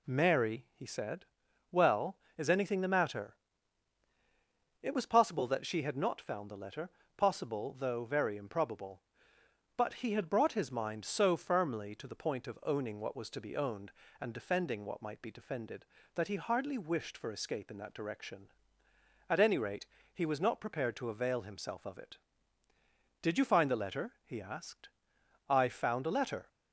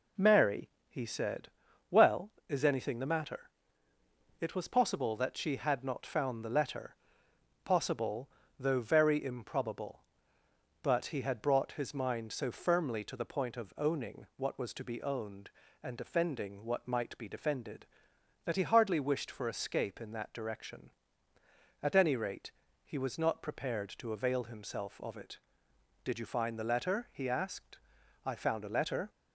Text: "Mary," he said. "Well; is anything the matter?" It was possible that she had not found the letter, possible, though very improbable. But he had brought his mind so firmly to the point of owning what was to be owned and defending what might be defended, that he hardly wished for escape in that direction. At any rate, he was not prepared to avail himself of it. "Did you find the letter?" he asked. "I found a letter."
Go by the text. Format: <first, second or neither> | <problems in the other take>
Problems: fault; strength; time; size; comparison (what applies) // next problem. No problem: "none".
neither | none